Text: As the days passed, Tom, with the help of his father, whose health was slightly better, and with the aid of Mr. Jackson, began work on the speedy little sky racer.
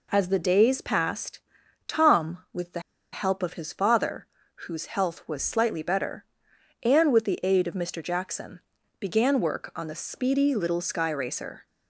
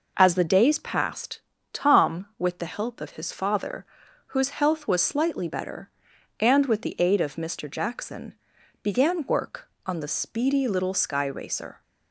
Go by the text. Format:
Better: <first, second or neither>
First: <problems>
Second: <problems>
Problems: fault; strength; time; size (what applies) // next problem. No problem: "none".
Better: second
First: pauses between "the" and "help"; slight; at 2.7 s; 0.33 s long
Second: none